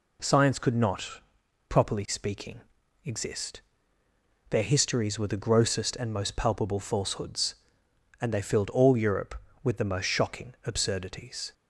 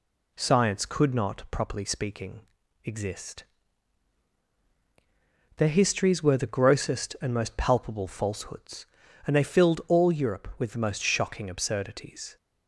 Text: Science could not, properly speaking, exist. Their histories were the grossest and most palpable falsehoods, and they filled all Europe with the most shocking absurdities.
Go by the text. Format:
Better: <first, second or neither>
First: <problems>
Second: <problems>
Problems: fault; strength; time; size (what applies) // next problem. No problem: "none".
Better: neither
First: none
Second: none